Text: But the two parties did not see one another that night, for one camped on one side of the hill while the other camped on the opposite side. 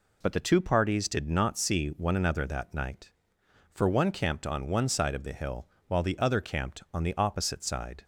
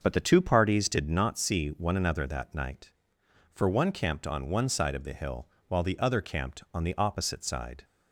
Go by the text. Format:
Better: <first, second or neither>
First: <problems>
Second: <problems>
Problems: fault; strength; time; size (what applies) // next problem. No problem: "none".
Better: first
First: pauses between "hill" and "while"; slight; at 5.6 s; 0.20 s long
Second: starts louder than the rest; until 1.2 s; 6 dB // pauses between "hill" and "while"; slight; at 5.4 s; 0.20 s long